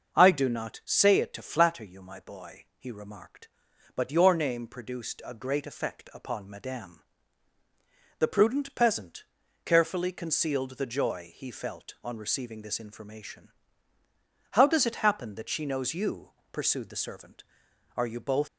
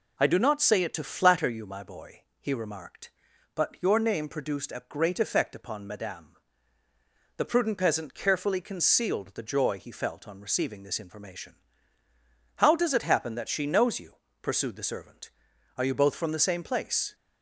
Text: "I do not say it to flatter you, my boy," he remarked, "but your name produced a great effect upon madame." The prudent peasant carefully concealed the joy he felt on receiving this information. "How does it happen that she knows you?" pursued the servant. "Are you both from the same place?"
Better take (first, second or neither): second